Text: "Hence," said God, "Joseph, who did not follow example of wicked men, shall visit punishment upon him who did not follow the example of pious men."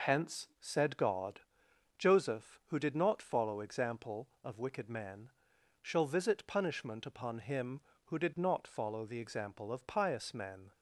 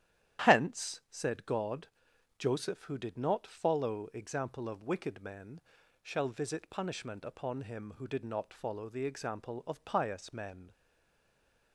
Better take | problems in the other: first | starts louder than the rest; strong; until 1.5 s; 11.5 dB // stays silent after the last word; from 10.7 s on; 1.0 s long

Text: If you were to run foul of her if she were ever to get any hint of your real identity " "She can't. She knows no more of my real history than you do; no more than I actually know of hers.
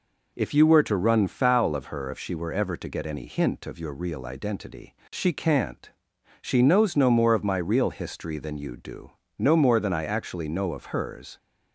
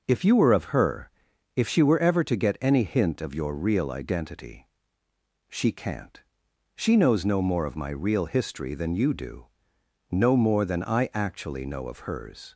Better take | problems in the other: first | starts louder than the rest; until 1.0 s; 6.5 dB // skips "to run foul"; at 0.5 s // pauses between "her" and "if"; noticeable; at 1.0 s; 0.46 s long

